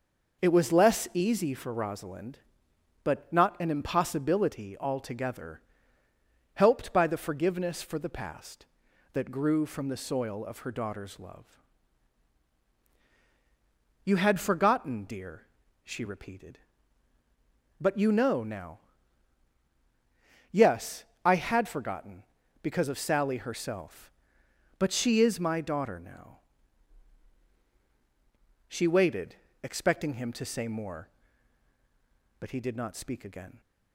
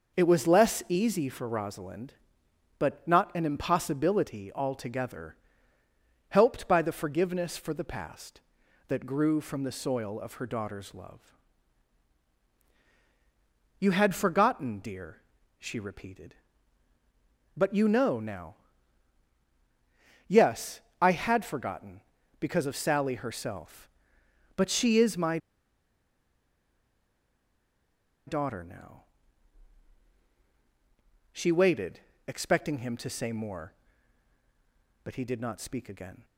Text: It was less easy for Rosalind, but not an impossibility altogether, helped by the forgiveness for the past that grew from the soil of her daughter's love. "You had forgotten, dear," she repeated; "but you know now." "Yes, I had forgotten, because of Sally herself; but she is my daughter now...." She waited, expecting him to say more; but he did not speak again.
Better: first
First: none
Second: pauses between "my" and "daughter"; strong; at 25.3 s; 2.8 s long

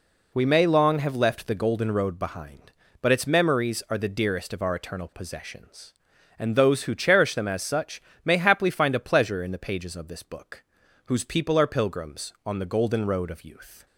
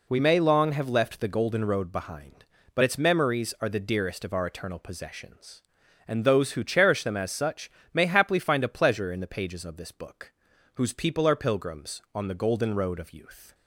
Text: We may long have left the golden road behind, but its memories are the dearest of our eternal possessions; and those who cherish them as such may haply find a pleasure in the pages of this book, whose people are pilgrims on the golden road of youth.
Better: neither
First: pauses between "such" and "may"; slight; at 8.0 s; 0.24 s long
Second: pauses between "such" and "may"; slight; at 7.6 s; 0.24 s long

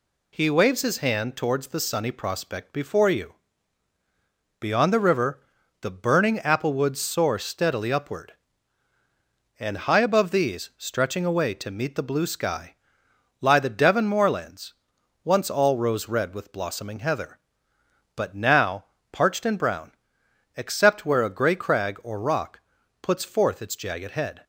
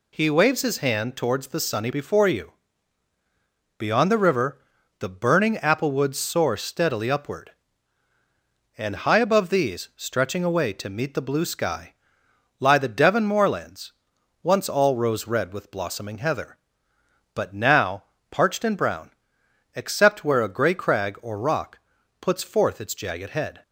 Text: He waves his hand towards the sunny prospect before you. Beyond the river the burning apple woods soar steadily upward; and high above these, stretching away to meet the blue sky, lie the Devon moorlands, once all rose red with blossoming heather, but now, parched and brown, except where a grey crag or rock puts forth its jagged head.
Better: first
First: pauses between "river" and "the"; at 5.4 s; 0.38 s long // pauses between "rock" and "puts"; at 22.5 s; 0.44 s long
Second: skips "prospect"; at 1.9 s // pauses between "river" and "the"; at 4.6 s; 0.38 s long // pauses between "rock" and "puts"; at 21.7 s; 0.44 s long

